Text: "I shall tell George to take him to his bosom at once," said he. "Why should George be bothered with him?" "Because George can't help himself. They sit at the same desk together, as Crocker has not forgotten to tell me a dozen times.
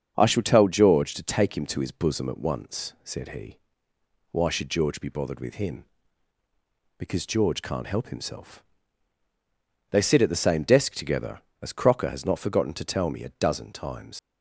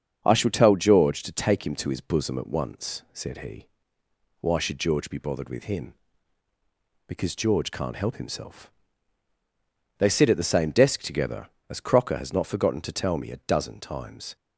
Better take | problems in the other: second | starts louder than the rest; strong; until 1.1 s; 7 dB; strong in the second // leaves "times" unfinished; at 14.1 s; 85 ms

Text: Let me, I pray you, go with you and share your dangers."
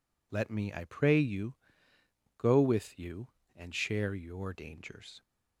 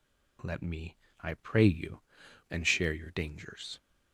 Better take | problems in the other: first | skips "go with you"; at 2.2 s

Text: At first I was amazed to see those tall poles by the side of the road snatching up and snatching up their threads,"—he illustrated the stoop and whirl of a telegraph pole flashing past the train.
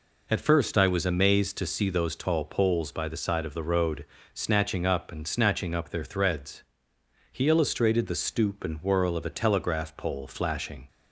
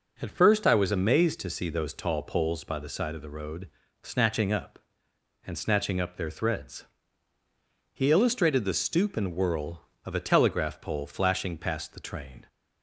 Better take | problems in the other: second | pauses between "road" and "snatching"; slight; at 4.0 s; 0.28 s long; slight in the second // stops before "past the train"; at 10.8 s

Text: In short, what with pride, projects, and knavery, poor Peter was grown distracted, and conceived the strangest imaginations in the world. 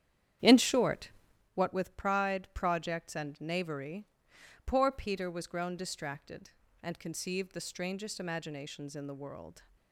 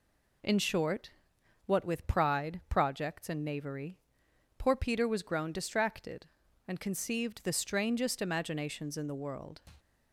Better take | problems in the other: second | starts louder than the rest; strong; until 1.5 s; 9.5 dB

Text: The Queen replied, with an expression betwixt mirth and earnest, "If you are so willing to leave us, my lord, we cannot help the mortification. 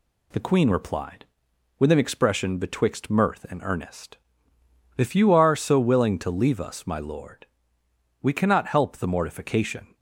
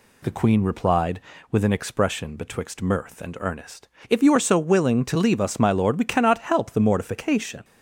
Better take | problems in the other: neither | none

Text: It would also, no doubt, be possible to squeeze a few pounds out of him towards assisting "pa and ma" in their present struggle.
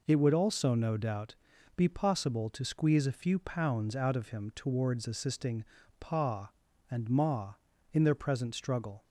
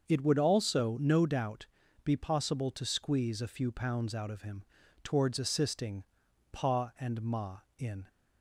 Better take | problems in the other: first | starts louder than the rest; until 1.1 s; 6.5 dB // pauses between "him" and "towards"; at 4.6 s; 0.38 s long // pauses between "assisting" and "pa"; noticeable; at 6.0 s; 0.48 s long; slight in the first // stops before "their present struggle"; at 8.0 s

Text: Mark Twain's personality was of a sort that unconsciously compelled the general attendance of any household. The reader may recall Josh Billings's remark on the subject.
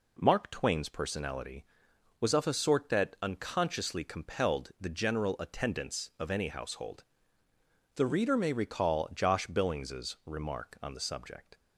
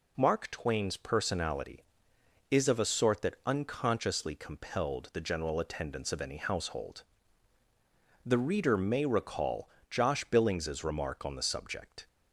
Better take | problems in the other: first | says "is" for "was"; at 2.4 s // pauses between "recall" and "Josh"; slight; at 9.6 s; 0.20 s long

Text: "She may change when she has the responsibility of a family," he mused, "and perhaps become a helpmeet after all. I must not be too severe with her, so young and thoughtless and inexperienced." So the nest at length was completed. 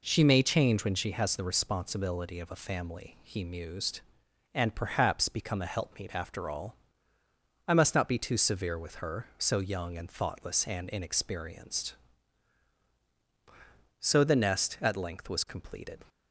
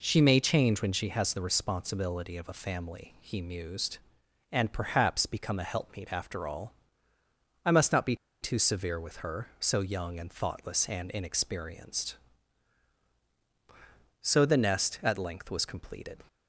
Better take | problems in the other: first | pauses between "be" and "too"; slight; at 8.1 s; 0.26 s long

